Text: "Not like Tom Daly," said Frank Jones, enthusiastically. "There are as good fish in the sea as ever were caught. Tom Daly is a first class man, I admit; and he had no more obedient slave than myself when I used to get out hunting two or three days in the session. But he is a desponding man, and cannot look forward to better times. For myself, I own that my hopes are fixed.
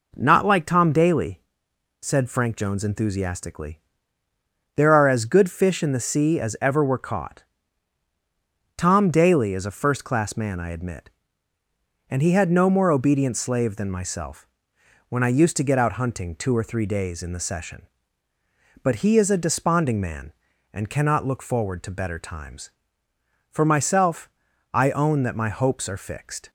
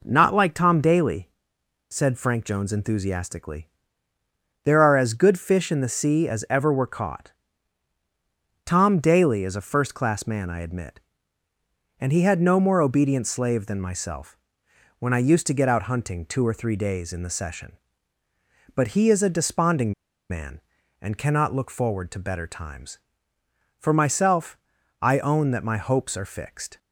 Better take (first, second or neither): first